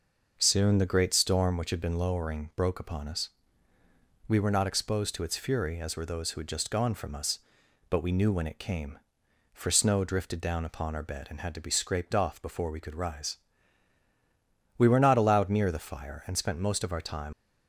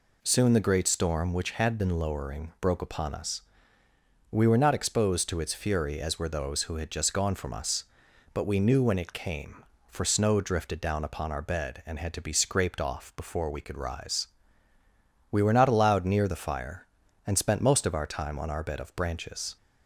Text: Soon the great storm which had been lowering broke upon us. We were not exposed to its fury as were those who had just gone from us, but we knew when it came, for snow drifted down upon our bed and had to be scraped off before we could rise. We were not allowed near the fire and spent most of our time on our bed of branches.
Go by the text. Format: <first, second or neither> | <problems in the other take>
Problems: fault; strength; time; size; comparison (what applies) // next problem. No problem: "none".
second | stops before "on our bed of branches"; at 17.3 s